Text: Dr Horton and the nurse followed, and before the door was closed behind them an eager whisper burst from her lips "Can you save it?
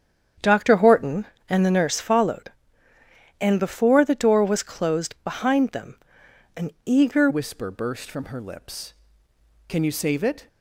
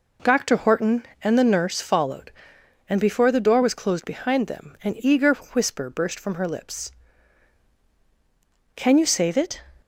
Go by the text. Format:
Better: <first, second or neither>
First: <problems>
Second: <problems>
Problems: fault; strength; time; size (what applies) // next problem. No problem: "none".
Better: second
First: starts louder than the rest; strong; until 1.6 s; 8.5 dB // pauses between "them" and "an"; noticeable; at 5.9 s; 0.58 s long // changes voice at "whisper"; from 7.2 s on; 3.2 s long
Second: none